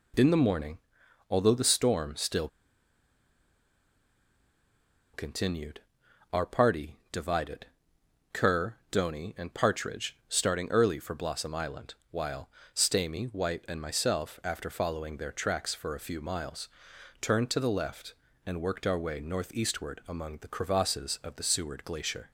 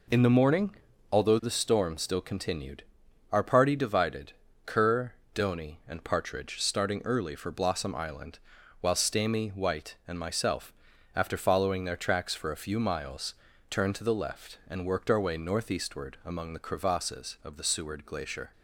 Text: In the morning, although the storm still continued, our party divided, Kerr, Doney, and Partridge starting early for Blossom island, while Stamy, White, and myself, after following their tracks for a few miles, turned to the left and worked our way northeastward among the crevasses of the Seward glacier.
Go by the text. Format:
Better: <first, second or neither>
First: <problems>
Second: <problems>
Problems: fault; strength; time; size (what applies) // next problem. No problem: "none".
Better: second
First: pauses between "still" and "continued"; strong; at 2.4 s; 2.6 s long // pauses between "party" and "divided"; slight; at 6.9 s; 0.16 s long // pauses between "while" and "Stamy"; slight; at 12.4 s; 0.24 s long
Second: none